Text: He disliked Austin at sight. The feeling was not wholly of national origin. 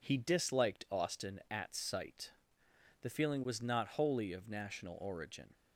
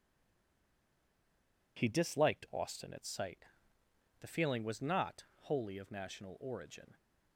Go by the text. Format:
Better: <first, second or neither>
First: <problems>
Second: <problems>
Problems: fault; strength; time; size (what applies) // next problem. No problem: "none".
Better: first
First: none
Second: stays silent before the first word; noticeable; until 1.7 s; 1.7 s long // pauses between "not" and "wholly"; slight; at 5.2 s; 0.16 s long